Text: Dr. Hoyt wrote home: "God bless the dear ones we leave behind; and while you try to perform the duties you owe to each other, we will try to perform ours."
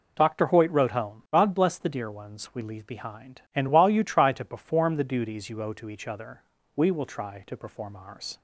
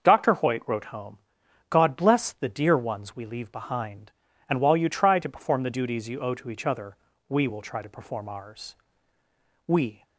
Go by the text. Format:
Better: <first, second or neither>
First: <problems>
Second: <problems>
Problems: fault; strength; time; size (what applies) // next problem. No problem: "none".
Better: first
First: none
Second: starts louder than the rest; until 1.0 s; 6.5 dB // goes on to say "We"; slight; from 9.6 s on; 0.38 s long